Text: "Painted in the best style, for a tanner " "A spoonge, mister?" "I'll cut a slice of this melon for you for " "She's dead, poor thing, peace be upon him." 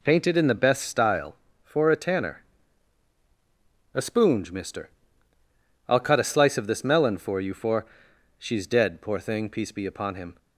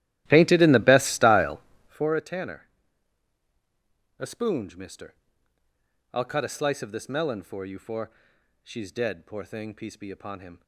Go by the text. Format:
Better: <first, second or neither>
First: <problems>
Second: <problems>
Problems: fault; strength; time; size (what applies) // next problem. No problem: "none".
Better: first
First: none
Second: starts louder than the rest; strong; until 2.2 s; 14.5 dB